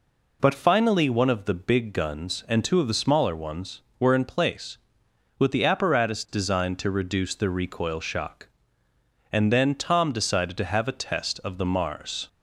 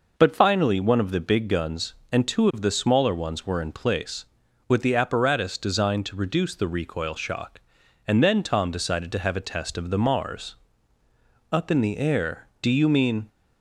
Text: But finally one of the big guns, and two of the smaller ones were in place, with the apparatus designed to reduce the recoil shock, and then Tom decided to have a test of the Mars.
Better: first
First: none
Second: goes on to say "Up in the air do you mean"; strong; from 11.5 s on; 1.7 s long

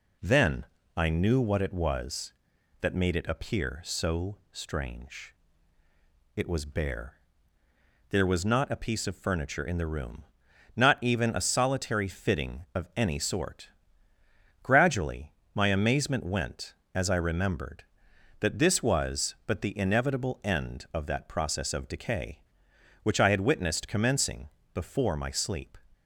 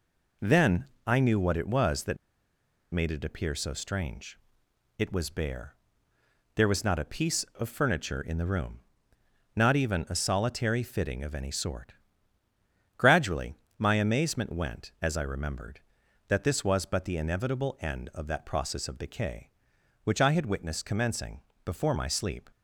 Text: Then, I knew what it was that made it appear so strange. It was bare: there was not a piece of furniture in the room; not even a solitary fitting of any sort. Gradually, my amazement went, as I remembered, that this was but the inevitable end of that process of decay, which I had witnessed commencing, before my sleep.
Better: first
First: none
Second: pauses between "that" and "made"; noticeable; at 2.1 s; 0.76 s long

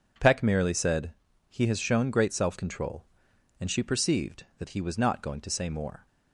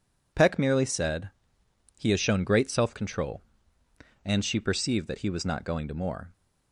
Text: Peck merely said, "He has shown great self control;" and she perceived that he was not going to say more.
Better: first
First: none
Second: skips "say"; at 5.9 s

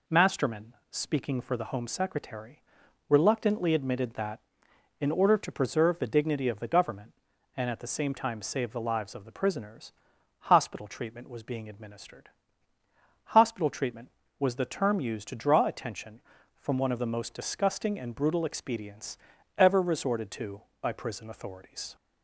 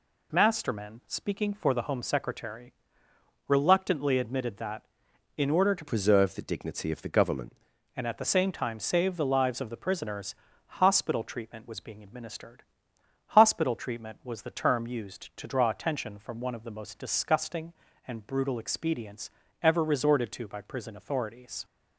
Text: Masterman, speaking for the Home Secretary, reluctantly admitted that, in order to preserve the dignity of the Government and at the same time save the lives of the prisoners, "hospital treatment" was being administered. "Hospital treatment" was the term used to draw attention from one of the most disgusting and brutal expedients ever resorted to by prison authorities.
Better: first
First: pauses between "expedients" and "ever"; at 19.1 s; 0.40 s long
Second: changes voice from "preserve" to "Government"; from 5.8 to 7.5 s; 1.7 s long // pauses between "expedients" and "ever"; slight; at 19.3 s; 0.32 s long

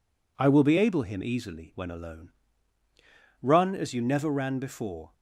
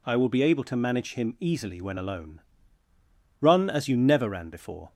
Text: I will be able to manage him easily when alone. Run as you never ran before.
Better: second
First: skips "to manage"; at 1.0 s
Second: none

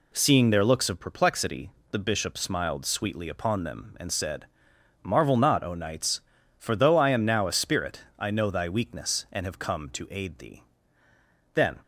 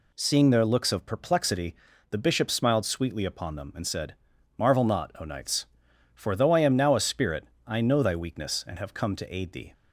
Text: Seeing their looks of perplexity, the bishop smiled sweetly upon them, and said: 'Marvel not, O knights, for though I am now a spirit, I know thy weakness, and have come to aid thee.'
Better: second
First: goes on to say "Then"; slight; from 11.5 s on; 0.26 s long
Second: none

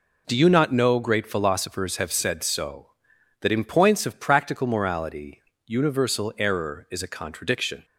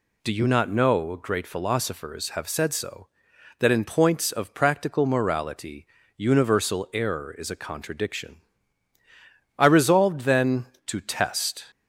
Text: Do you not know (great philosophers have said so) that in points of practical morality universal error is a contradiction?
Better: first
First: pauses between "morality" and "universal"; slight; at 5.4 s; 0.24 s long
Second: pauses between "morality" and "universal"; slight; at 5.8 s; 0.32 s long // goes on to say "I resolved then to test"; strong; from 9.5 s on; 2.1 s long

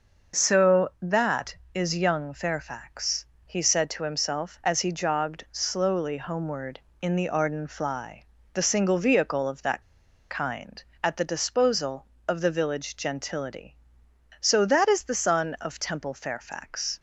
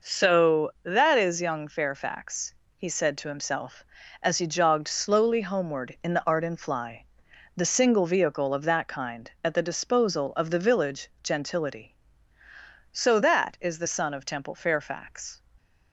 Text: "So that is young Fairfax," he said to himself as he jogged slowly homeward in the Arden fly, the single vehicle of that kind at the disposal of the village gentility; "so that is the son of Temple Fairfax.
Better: second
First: pauses between "that" and "kind"; noticeable; at 9.8 s; 0.47 s long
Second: none

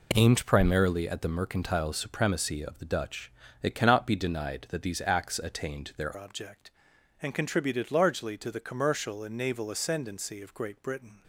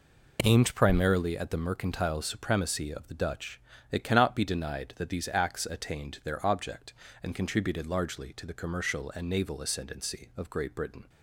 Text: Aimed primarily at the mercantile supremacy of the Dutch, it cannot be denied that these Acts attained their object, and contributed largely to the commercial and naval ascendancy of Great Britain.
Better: second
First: changes voice at "object"; from 6.1 s on; 5.1 s long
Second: none

